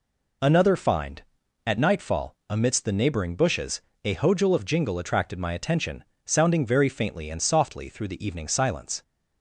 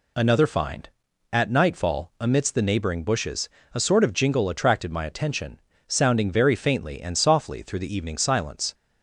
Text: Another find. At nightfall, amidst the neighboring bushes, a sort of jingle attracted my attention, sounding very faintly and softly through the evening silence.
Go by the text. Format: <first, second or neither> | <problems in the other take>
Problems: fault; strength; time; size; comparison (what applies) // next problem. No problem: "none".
second | says "hojul" for "sort"; at 4.1 s